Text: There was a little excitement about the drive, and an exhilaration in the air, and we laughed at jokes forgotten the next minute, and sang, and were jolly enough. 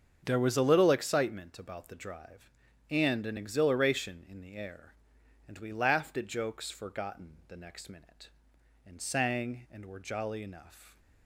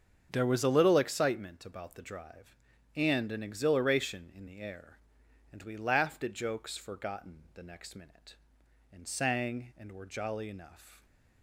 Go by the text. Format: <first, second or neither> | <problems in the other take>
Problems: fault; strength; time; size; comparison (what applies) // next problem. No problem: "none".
neither | starts louder than the rest; strong; the same in both